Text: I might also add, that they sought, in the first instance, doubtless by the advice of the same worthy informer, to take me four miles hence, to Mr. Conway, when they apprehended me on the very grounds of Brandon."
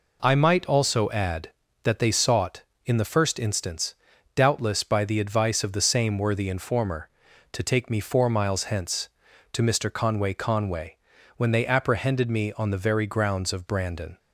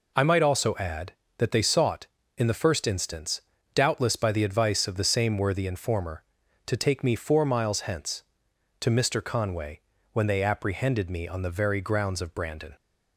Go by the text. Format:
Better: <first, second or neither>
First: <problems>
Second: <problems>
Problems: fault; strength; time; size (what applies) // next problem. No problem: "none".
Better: second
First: says "Conway" twice; at 10.3 s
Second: none